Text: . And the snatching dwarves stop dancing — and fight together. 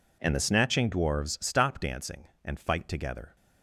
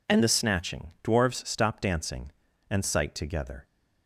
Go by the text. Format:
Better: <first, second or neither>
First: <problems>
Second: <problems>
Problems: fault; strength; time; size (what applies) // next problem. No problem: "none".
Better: first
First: none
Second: says "sight" for "fight"; at 2.8 s